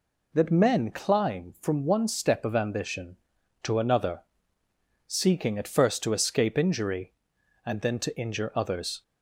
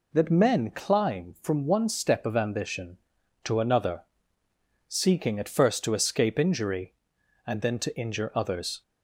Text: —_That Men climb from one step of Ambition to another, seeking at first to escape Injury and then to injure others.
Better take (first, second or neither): neither